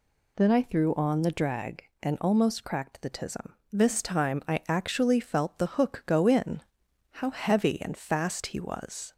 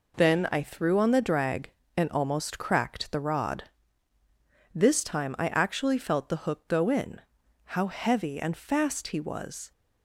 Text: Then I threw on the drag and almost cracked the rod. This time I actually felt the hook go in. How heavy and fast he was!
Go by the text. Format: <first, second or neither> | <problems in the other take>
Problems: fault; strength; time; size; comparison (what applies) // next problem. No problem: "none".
second | says "tism" for "rod"; at 3.1 s